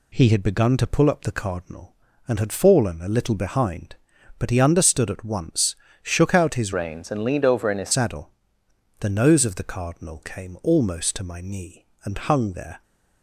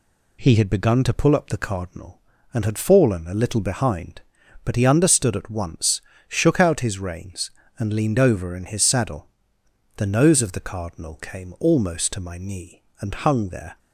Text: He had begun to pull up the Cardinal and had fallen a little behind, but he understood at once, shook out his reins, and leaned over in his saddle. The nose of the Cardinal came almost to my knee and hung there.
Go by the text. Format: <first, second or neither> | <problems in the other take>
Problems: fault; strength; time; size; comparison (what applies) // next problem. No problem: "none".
second | changes voice from "reins" to "his"; from 6.7 to 7.9 s; 1.2 s long